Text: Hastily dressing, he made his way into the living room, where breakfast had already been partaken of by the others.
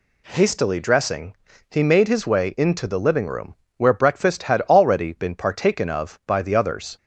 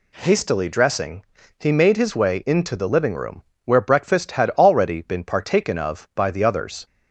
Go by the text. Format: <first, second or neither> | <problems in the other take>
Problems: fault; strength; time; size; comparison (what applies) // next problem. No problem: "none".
neither | none